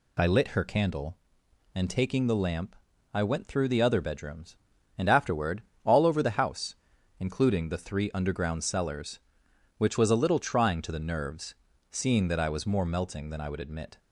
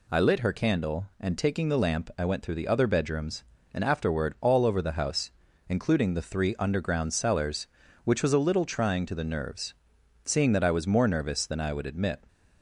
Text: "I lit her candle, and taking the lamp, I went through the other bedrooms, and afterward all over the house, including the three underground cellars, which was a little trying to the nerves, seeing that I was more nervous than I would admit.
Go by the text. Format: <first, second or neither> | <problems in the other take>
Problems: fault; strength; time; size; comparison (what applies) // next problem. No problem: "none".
second | pauses between "afterward" and "all"; slight; at 5.6 s; 0.22 s long // says "melting" for "nervous"; at 12.8 s